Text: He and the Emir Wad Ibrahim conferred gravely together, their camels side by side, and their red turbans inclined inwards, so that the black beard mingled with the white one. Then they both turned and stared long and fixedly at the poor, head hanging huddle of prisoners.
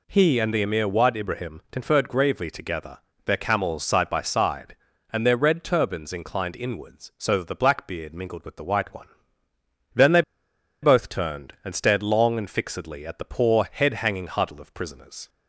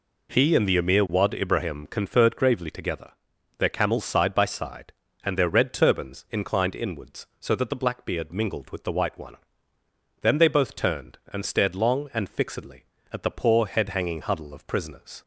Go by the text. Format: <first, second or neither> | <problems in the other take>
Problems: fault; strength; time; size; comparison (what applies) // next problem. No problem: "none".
second | pauses between "they" and "both"; noticeable; at 10.2 s; 0.60 s long